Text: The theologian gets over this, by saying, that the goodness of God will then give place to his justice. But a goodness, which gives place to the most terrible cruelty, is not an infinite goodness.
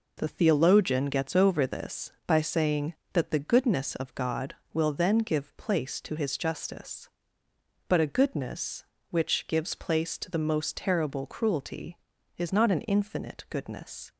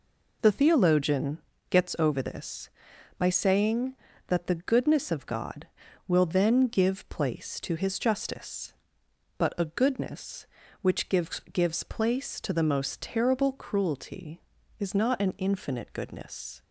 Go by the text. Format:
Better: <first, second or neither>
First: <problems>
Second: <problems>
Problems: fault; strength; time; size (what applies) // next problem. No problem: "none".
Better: first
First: none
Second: pauses between "theologian" and "gets"; slight; at 1.3 s; 0.30 s long // says "gives" twice; at 11.5 s